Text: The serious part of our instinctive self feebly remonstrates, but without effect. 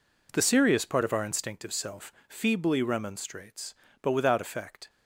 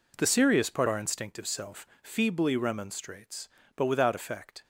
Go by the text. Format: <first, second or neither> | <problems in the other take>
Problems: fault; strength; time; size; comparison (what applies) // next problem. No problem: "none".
first | skips "of"; at 0.8 s